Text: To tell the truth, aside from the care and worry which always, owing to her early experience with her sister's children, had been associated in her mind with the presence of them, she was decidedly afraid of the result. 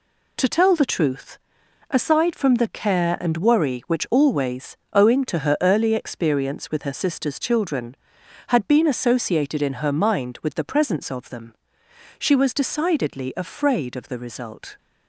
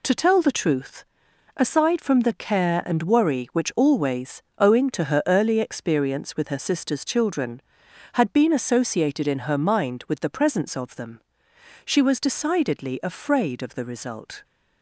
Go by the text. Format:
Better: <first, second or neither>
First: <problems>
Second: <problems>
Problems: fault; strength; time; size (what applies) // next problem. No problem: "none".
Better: neither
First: none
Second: none